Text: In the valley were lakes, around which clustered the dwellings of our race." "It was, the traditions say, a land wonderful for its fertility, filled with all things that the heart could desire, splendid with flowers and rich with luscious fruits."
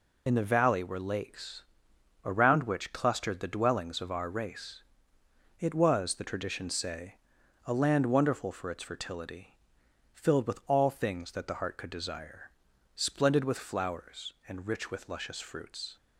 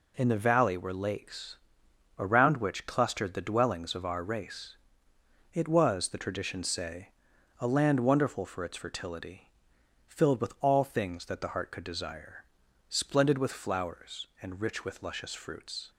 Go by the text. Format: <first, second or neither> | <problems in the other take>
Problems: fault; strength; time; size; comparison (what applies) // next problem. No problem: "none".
second | loses the start of "In"; at 0.2 s; 40 ms